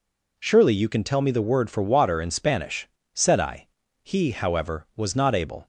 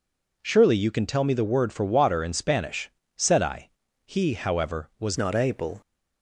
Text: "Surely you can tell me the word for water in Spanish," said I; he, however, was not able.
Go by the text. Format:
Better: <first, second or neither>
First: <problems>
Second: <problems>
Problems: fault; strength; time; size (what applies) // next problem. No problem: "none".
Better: first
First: none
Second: changes voice at "not"; from 5.1 s on; 0.7 s long